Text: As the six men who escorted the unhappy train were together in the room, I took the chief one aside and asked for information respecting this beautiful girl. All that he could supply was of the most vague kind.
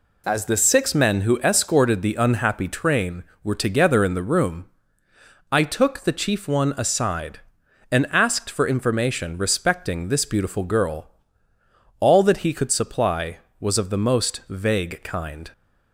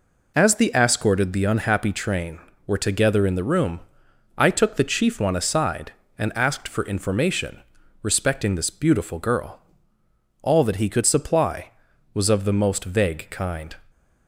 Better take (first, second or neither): first